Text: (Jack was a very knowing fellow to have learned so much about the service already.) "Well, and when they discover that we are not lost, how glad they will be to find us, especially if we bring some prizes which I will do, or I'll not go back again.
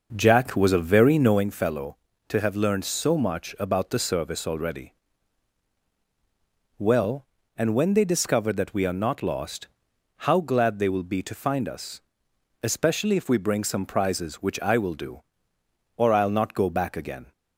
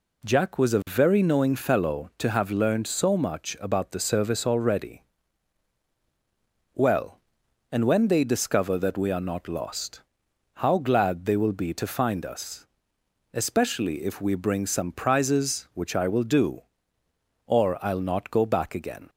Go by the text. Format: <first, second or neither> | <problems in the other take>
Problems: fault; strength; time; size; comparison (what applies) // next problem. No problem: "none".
second | starts louder than the rest; noticeable; until 1.5 s; 5.5 dB